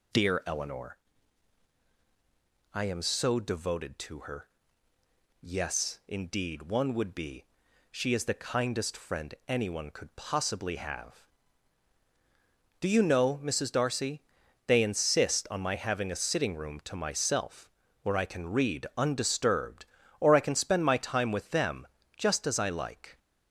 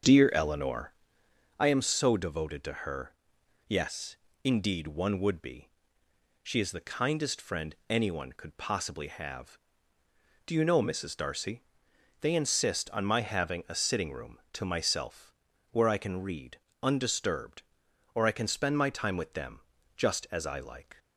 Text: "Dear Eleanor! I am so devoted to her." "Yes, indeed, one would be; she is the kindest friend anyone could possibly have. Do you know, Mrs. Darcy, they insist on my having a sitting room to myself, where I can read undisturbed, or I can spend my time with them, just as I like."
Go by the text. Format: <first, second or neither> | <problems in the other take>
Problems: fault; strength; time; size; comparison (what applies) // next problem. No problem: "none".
first | starts louder than the rest; until 1.6 s; 7 dB // pauses between "read" and "undisturbed"; slight; at 16.5 s; 0.24 s long